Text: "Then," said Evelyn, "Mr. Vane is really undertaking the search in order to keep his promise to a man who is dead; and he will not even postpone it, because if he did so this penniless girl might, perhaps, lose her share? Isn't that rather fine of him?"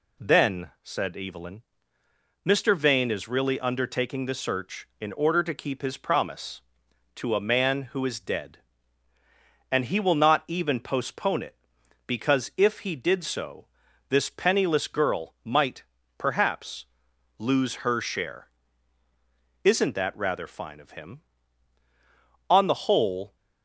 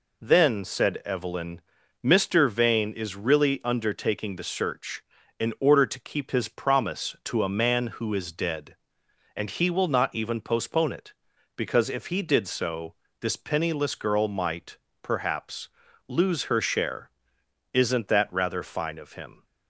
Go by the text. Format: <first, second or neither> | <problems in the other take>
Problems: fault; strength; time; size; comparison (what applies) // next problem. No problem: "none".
second | pauses between "so" and "this"; at 13.6 s; 0.42 s long; slight in the second // goes on to say "On the whole"; noticeable; from 22.4 s on; 0.86 s long